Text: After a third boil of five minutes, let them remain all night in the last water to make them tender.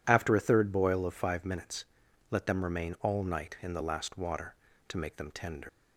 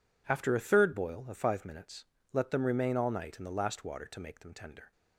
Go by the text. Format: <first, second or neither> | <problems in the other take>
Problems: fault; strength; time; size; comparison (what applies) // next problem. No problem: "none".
second | leaves "tender" unfinished; at 5.6 s; 80 ms